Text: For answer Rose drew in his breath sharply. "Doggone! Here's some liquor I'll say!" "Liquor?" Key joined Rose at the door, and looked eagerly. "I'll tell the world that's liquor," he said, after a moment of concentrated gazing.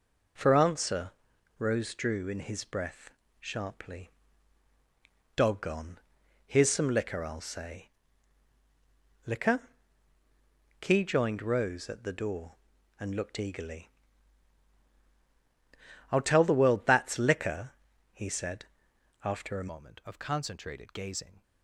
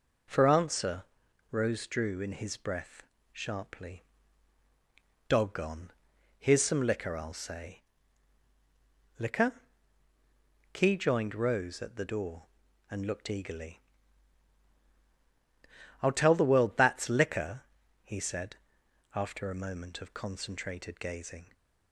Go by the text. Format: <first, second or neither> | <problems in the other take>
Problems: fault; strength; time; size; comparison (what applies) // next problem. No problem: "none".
second | pauses between "answer" and "Rose"; noticeable; at 1.1 s; 0.46 s long; noticeable in the second // pauses between "breath" and "sharply"; slight; at 3.0 s; 0.32 s long; slight in the second // changes voice at "moment"; from 19.7 s on; 1.7 s long